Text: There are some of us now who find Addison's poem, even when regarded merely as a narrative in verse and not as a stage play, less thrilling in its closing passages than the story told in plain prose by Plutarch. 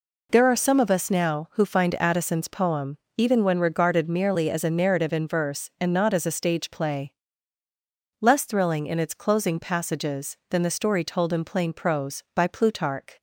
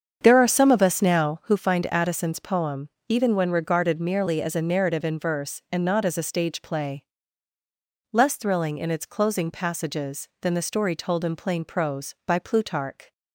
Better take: first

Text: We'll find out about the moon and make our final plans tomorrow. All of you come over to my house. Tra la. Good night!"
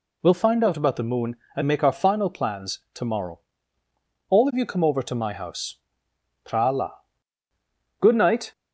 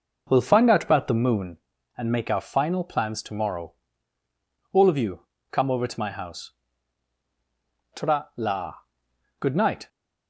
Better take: first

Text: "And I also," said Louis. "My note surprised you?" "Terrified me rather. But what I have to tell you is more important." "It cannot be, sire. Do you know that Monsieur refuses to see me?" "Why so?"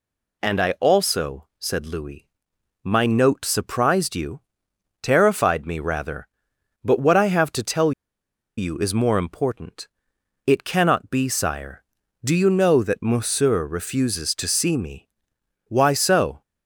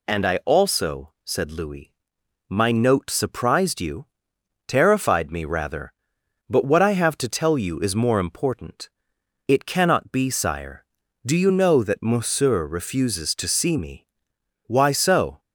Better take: second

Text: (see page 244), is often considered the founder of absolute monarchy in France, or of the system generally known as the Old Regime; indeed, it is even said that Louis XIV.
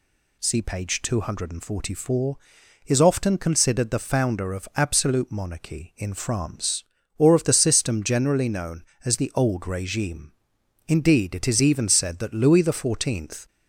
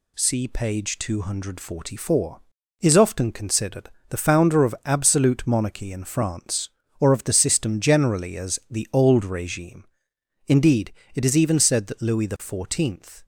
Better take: first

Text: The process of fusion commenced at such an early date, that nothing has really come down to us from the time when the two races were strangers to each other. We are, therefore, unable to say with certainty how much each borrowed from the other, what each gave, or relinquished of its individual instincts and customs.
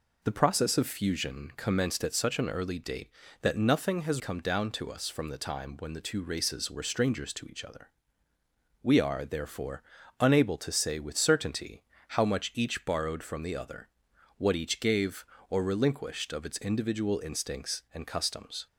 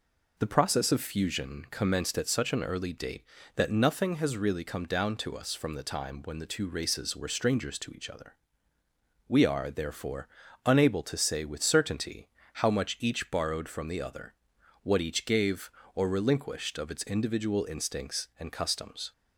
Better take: second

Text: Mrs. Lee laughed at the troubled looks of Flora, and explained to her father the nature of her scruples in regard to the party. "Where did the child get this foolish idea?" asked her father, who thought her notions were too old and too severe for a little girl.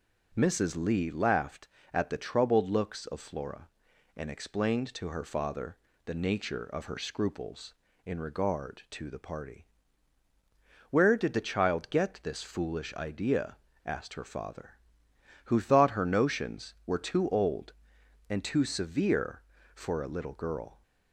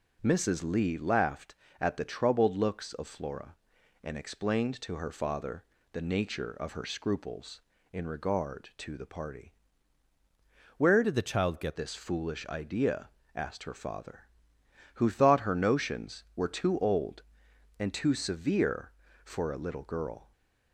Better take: first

